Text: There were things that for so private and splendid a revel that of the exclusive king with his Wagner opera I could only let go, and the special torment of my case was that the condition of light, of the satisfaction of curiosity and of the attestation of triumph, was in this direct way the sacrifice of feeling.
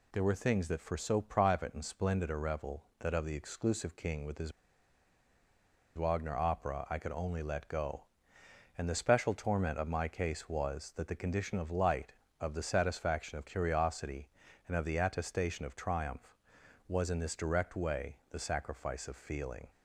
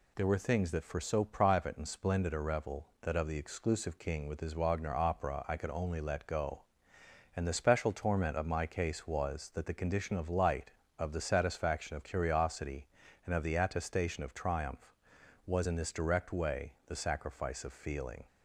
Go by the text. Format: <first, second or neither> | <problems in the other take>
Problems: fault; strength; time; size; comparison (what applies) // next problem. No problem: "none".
second | pauses between "his" and "Wagner"; strong; at 4.5 s; 1.4 s long